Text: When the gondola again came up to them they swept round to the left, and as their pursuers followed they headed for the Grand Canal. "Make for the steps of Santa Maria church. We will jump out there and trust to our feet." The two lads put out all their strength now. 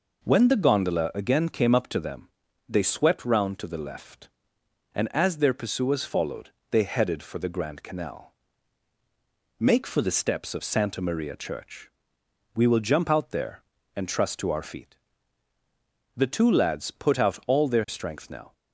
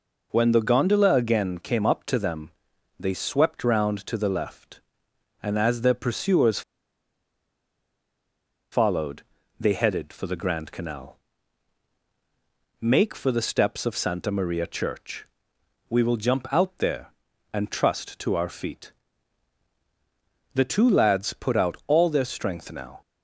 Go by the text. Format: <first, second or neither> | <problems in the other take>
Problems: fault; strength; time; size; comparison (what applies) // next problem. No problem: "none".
first | pauses between "them" and "they"; noticeable; at 2.5 s; 0.46 s long; also in the first // pauses between "pursuers" and "followed"; strong; at 6.6 s; 2.1 s long // pauses between "followed" and "they"; slight; at 9.2 s; 0.36 s long; slight in the first